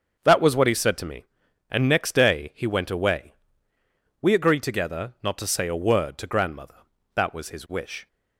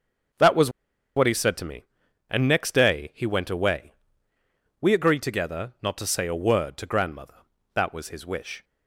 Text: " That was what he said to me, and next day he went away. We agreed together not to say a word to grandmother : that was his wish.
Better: first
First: starts louder than the rest; until 1.2 s; 7 dB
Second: starts louder than the rest; until 1.8 s; 7 dB // pauses between "was" and "what"; at 0.7 s; 0.45 s long

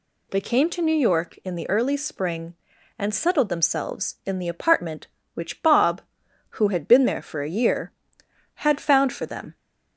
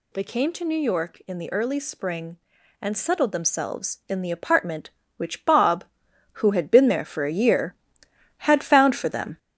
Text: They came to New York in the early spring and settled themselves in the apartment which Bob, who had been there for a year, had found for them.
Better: first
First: none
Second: gets louder; noticeable; throughout; 5 dB

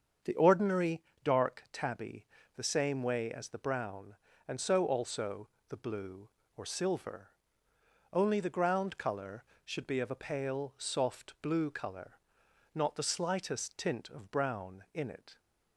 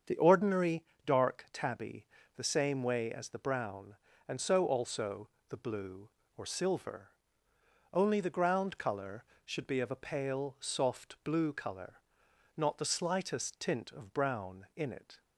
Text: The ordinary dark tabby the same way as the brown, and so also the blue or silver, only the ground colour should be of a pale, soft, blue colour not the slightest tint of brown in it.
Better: neither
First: starts louder than the rest; strong; until 1.4 s; 7.5 dB // pauses between "ordinary" and "dark"; slight; at 1.0 s; 0.22 s long // pauses between "tabby" and "the"; slight; at 2.2 s; 0.30 s long // pauses between "also" and "the"; slight; at 5.4 s; 0.22 s long // pauses between "colour" and "not"; noticeable; at 12.1 s; 0.56 s long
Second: starts louder than the rest; strong; until 1.2 s; 7.5 dB // pauses between "ordinary" and "dark"; slight; at 0.8 s; 0.22 s long // pauses between "tabby" and "the"; slight; at 2.0 s; 0.30 s long // pauses between "also" and "the"; slight; at 5.2 s; 0.22 s long // pauses between "colour" and "not"; noticeable; at 11.9 s; 0.56 s long

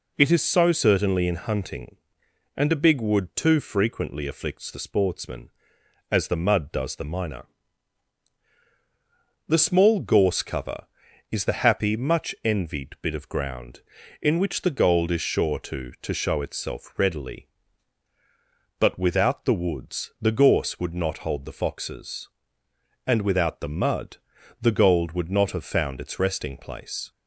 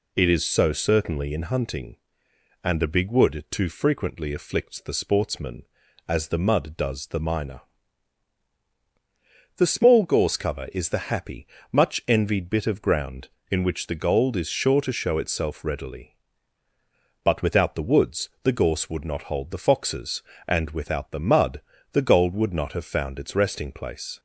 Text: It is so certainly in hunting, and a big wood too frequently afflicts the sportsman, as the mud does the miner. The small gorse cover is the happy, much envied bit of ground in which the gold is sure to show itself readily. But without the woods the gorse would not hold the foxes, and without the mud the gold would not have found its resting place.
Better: second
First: says "to" twice; at 16.0 s // pauses between "mud" and "the"; at 24.1 s; 0.42 s long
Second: pauses between "mud" and "the"; slight; at 21.6 s; 0.30 s long

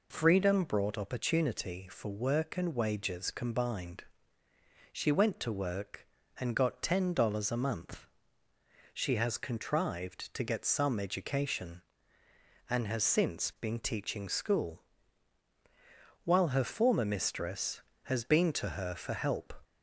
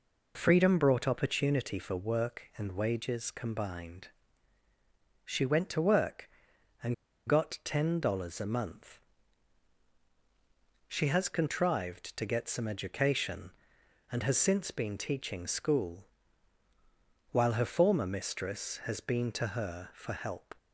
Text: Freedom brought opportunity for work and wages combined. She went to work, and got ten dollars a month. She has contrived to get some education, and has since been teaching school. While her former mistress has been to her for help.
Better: first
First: none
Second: pauses between "and" and "got"; slight; at 6.9 s; 0.32 s long

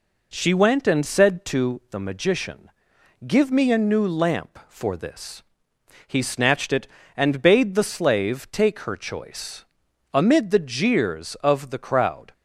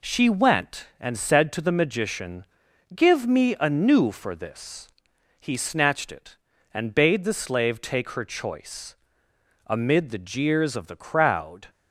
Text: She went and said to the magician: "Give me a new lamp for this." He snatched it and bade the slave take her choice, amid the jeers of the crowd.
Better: first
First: none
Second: skips "lamp"; at 4.0 s

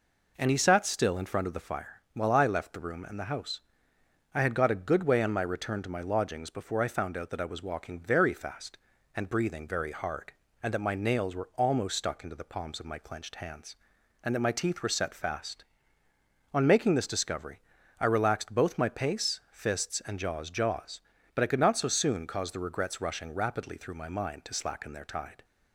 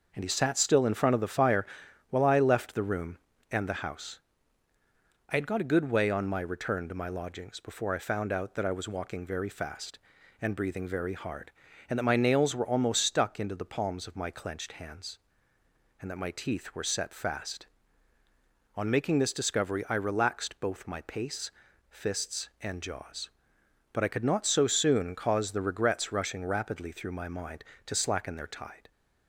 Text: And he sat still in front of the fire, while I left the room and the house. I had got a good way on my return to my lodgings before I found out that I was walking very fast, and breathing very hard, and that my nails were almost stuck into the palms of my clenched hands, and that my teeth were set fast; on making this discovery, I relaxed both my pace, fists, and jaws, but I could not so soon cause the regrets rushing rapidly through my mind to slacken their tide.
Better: second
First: says "jaws" twice; at 20.5 s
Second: none

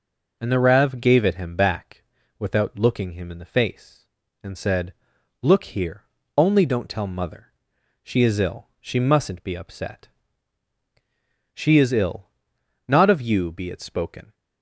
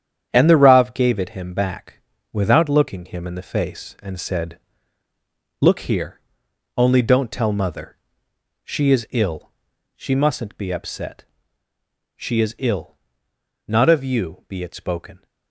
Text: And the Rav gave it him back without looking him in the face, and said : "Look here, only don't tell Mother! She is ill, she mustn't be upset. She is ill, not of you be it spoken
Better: first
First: pauses between "back" and "without"; slight; at 2.0 s; 0.36 s long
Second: gets quieter; strong; throughout; 7.5 dB // pauses between "back" and "without"; slight; at 1.9 s; 0.32 s long

